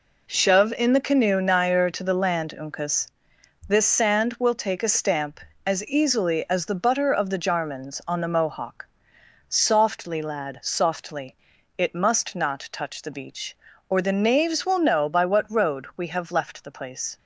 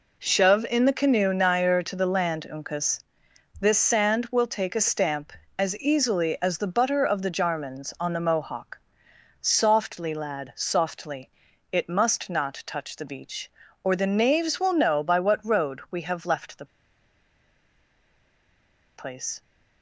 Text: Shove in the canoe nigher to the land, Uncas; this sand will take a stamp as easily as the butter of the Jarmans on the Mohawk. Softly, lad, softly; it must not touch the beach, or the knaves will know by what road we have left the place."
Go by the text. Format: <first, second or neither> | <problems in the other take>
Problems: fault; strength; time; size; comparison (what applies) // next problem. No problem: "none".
first | pauses between "the" and "place"; strong; at 16.6 s; 2.2 s long